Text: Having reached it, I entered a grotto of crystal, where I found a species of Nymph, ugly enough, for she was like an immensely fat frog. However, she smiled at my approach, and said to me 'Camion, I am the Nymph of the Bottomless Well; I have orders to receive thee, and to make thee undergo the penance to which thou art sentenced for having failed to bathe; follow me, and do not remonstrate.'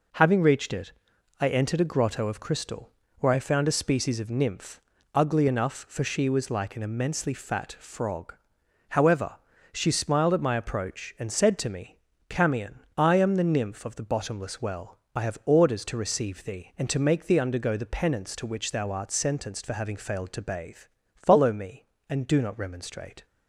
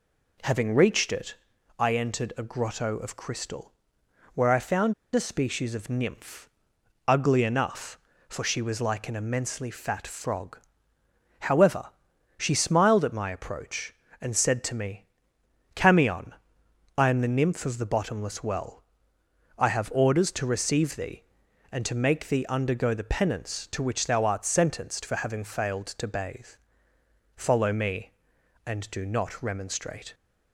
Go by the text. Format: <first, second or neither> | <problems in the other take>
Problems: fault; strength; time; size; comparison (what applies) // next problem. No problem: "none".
first | pauses between "found" and "a"; slight; at 4.9 s; 0.20 s long // pauses between "me" and "Camion"; noticeable; at 15.0 s; 0.68 s long; slight in the first